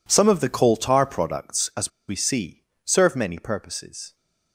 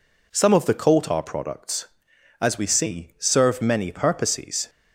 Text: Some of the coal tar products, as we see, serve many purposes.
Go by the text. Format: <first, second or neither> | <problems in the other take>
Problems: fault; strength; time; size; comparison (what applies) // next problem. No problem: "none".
second | pauses between "as" and "we"; slight; at 1.8 s; 0.18 s long